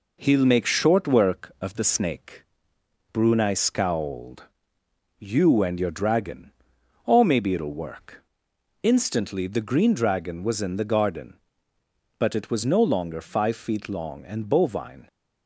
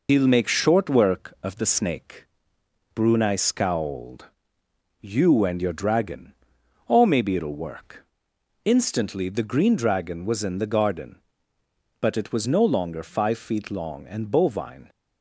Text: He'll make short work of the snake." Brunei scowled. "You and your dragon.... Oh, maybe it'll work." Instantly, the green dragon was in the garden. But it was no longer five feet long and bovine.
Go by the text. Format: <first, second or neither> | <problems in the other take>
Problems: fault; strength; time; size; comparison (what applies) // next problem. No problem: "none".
first | loses the start of "He'll"; at 0.0 s; 85 ms